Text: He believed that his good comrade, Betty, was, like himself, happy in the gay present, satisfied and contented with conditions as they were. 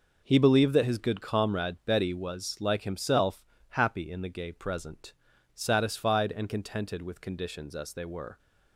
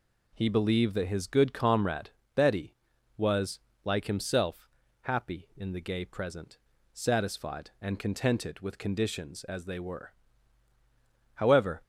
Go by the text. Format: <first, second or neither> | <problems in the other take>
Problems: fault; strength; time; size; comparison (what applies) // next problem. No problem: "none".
first | goes on to say "However"; slight; from 11.3 s on; 0.48 s long